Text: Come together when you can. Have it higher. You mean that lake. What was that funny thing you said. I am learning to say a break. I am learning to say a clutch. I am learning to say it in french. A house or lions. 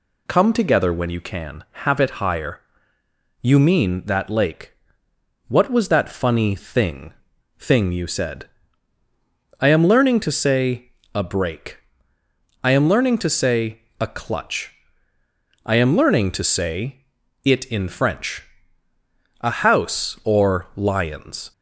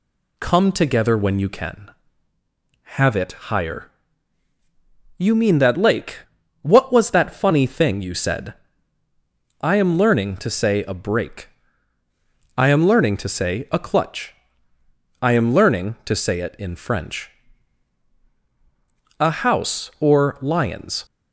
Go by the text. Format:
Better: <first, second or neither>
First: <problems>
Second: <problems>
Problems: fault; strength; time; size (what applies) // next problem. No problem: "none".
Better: second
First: says "thing" twice; at 7.5 s // pauses between "say" and "a"; slight; at 10.8 s; 0.24 s long // pauses between "say" and "a"; slight; at 13.7 s; 0.18 s long // pauses between "say" and "it"; at 17.0 s; 0.40 s long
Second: none